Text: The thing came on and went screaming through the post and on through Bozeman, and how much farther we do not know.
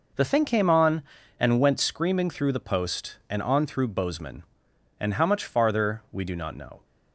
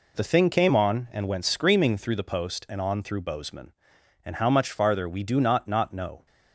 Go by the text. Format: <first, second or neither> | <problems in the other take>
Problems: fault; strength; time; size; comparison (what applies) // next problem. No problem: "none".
first | says "not" twice; at 5.6 s